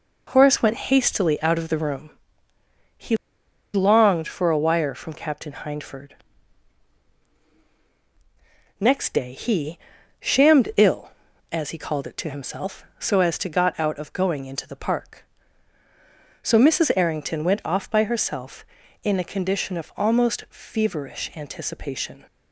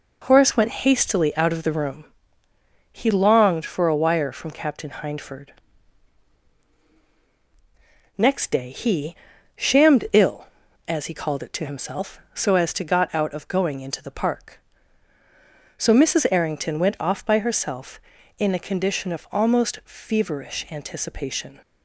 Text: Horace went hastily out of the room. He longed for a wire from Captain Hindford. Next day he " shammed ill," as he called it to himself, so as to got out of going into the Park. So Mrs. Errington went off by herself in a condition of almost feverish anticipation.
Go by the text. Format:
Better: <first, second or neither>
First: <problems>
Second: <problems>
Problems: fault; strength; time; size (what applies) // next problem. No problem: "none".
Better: second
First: pauses between "He" and "longed"; noticeable; at 3.1 s; 0.57 s long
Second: none